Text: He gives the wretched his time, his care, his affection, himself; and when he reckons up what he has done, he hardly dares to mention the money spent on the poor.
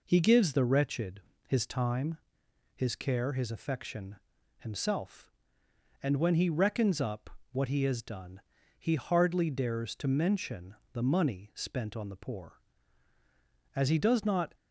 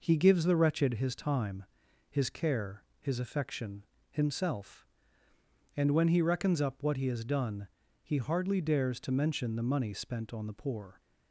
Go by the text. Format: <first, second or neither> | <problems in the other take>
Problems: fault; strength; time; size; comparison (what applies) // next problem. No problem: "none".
second | pauses between "wretched" and "his"; slight; at 1.2 s; 0.26 s long // pauses between "up" and "what"; slight; at 7.2 s; 0.22 s long // pauses between "mention" and "the"; slight; at 10.7 s; 0.18 s long // goes on to say "As he does not"; noticeable; from 13.7 s on; 0.80 s long